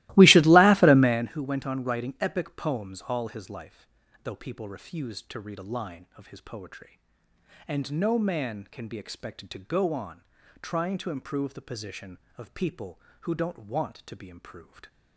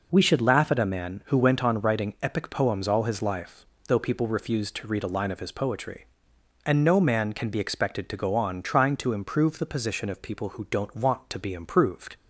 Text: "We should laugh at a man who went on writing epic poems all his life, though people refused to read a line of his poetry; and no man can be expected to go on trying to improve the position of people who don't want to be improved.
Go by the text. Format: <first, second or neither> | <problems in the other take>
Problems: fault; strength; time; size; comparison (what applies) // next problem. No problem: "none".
second | starts louder than the rest; strong; until 1.3 s; 19 dB // pauses between "on" and "trying"; at 10.2 s; 0.38 s long